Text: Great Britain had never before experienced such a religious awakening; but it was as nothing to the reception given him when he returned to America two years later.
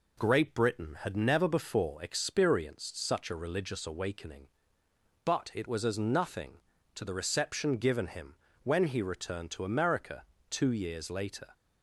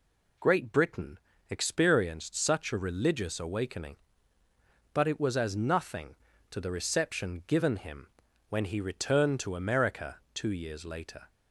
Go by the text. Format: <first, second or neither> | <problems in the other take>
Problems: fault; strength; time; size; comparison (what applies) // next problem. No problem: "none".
first | skips "had never before"; at 1.3 s // pauses between "him" and "when"; at 8.0 s; 0.42 s long; slight in the first // pauses between "America" and "two"; slight; at 10.1 s; 0.16 s long; slight in the first